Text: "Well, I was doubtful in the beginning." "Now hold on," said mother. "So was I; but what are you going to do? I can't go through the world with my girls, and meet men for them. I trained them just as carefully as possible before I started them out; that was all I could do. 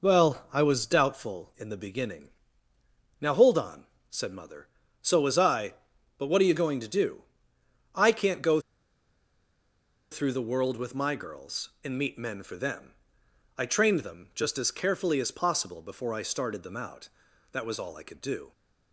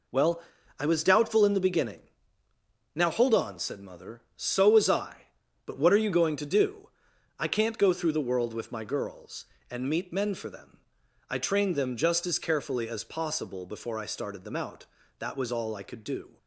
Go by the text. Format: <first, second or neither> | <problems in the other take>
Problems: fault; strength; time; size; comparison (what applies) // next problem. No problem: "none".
second | pauses between "go" and "through"; strong; at 8.6 s; 1.5 s long